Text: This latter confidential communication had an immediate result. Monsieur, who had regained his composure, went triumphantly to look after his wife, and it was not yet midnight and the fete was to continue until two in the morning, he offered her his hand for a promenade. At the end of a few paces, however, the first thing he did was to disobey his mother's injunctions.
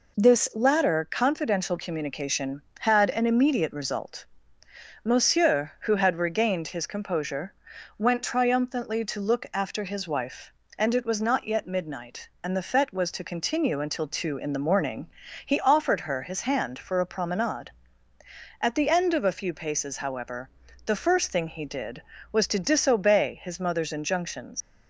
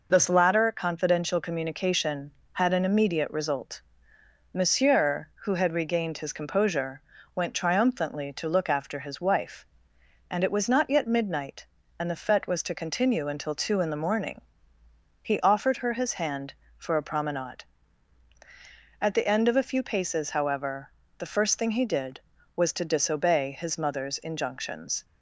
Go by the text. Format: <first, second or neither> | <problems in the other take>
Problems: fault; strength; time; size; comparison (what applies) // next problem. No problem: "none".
second | leaves "injunctions" unfinished; at 24.6 s; 100 ms